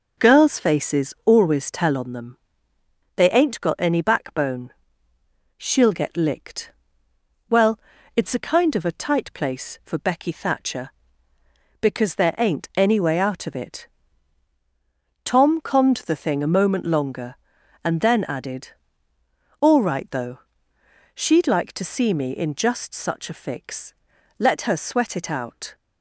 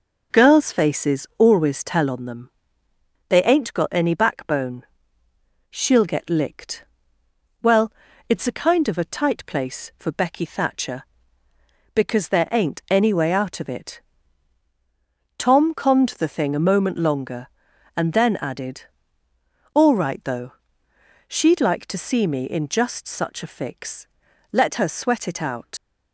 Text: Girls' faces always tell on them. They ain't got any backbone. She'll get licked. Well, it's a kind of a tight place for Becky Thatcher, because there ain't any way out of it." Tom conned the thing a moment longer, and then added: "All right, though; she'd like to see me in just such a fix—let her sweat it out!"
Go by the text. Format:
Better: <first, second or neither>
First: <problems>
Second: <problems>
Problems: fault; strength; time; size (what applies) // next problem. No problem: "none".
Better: first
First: none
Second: leaves "out" unfinished; at 25.7 s; 90 ms